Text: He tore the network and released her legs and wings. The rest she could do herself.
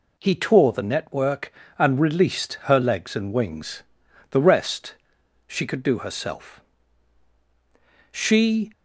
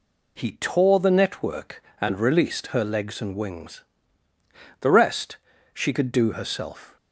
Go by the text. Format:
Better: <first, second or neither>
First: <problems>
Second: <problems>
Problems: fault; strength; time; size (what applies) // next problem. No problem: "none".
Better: second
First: pauses between "rest" and "she"; noticeable; at 4.9 s; 0.50 s long // goes on to say "She"; from 8.1 s on; 0.60 s long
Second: pauses between "rest" and "she"; slight; at 5.3 s; 0.34 s long